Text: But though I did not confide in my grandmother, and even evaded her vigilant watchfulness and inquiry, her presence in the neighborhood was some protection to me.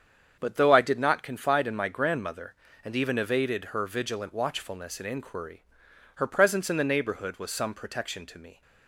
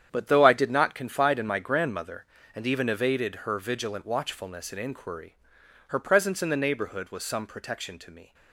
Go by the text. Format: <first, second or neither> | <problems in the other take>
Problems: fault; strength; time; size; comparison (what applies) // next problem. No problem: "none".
first | gets quieter; strong; throughout; 10.5 dB // starts louder than the rest; strong; until 1.1 s; 9 dB; strong in the first